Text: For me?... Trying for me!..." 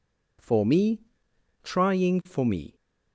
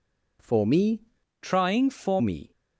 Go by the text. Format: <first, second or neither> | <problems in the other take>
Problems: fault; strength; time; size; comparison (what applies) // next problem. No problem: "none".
first | changes voice from "Trying" to "for"; from 1.4 to 2.1 s; 0.7 s long